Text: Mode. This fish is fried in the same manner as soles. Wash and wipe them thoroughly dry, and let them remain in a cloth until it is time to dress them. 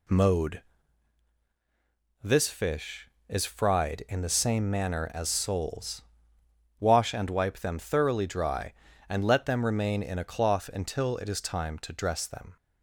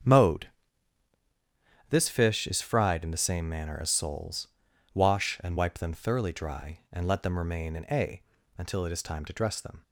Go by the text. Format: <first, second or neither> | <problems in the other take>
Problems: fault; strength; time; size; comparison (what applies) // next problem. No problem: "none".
first | starts louder than the rest; strong; until 2.4 s; 7.5 dB // skips "cloth"; at 8.3 s